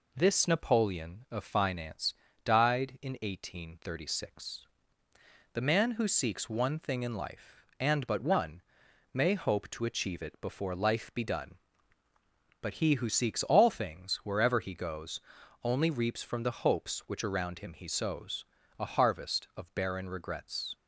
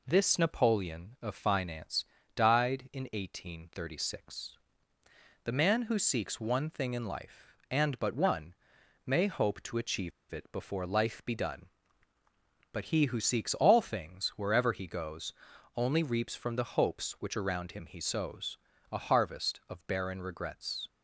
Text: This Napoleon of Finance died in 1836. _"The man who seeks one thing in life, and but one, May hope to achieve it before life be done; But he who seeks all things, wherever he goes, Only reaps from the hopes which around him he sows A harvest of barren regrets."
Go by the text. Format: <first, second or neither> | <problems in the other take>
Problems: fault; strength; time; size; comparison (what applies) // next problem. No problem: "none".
first | pauses between "Finance" and "died"; slight; at 2.0 s; 0.32 s long; slight in the first // pauses between "achieve" and "it"; slight; at 10.1 s; 0.20 s long // pauses between "sows" and "A"; slight; at 18.5 s; 0.32 s long; slight in the first